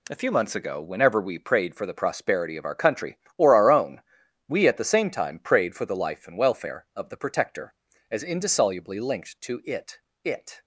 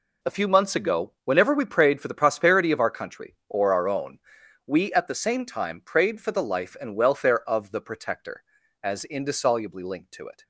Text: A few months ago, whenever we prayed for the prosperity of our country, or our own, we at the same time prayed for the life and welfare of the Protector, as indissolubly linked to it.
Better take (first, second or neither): second